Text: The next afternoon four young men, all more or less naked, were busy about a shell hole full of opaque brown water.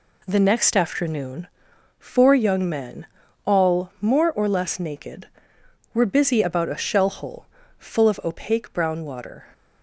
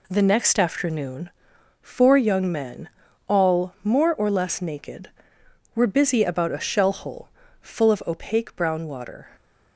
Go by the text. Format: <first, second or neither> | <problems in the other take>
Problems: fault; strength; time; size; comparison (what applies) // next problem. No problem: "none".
neither | pauses between "afternoon" and "four"; noticeable; the same in both // pauses between "hole" and "full"; slight; the same in both